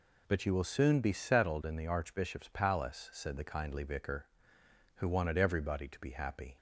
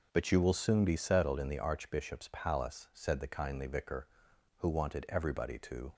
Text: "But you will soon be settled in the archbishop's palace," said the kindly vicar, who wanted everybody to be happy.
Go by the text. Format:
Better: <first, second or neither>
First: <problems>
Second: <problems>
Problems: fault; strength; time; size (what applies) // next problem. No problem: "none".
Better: first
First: none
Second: stops before "be happy"; at 5.9 s